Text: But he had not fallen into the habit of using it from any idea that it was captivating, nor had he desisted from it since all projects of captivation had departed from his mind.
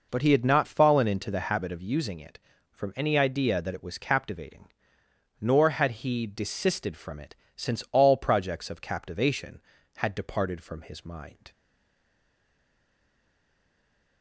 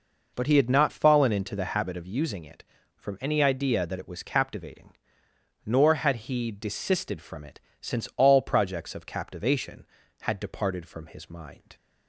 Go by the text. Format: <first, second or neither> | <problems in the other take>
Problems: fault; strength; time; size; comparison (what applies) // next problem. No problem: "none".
second | pauses between "it" and "since"; slight; at 7.3 s; 0.22 s long; slight in the second // stays silent after the last word; strong; from 11.5 s on; 2.7 s long